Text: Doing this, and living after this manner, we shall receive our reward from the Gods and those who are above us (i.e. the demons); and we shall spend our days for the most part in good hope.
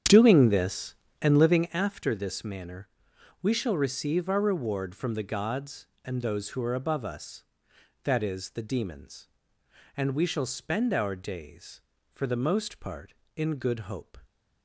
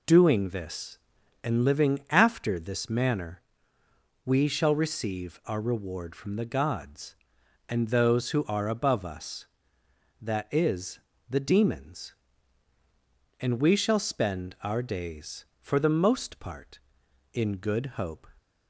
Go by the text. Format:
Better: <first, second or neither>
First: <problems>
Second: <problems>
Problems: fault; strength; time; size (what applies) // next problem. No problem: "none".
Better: second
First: starts louder than the rest; strong; until 1.8 s; 8.5 dB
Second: none